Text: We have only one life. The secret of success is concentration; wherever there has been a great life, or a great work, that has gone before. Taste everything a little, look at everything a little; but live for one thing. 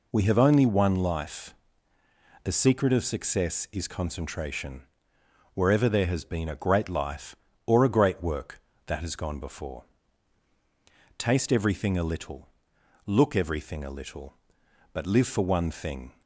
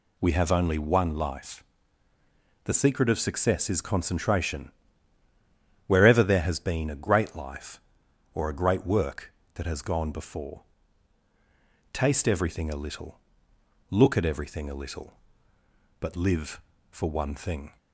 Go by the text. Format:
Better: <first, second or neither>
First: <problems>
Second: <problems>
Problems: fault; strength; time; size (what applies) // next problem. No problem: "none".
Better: second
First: skips "at"; at 13.3 s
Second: none